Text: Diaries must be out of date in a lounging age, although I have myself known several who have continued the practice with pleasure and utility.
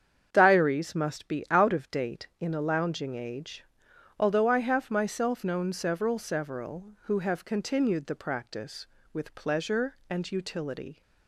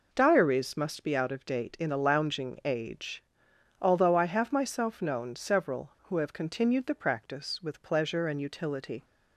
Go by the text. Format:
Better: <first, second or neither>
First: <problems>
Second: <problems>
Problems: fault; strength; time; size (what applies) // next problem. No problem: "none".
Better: second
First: starts louder than the rest; strong; until 1.3 s; 8 dB // says "several" twice; at 6.1 s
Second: none